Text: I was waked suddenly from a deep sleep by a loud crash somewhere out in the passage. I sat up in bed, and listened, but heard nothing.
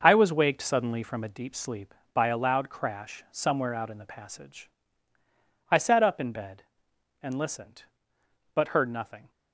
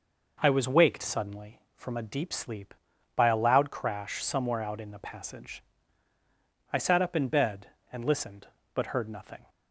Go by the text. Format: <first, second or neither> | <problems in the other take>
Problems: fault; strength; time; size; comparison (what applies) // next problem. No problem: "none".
second | gets quieter; strong; throughout; 8 dB